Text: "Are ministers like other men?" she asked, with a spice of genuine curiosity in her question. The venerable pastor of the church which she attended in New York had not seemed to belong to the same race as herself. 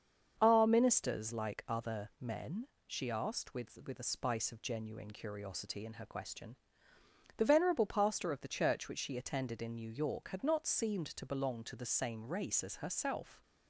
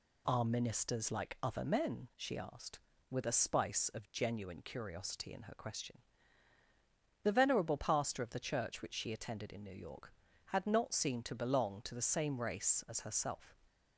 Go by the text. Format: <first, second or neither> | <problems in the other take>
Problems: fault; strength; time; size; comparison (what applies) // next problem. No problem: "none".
second | starts louder than the rest; until 1.4 s; 7 dB // says "with" twice; at 3.8 s